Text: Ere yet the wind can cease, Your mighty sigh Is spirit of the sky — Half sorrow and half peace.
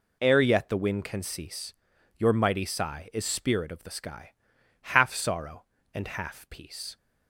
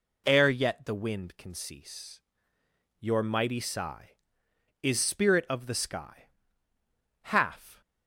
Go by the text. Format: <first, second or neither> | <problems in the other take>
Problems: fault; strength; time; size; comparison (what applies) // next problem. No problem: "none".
first | stops before "sorrow and half peace"; at 7.8 s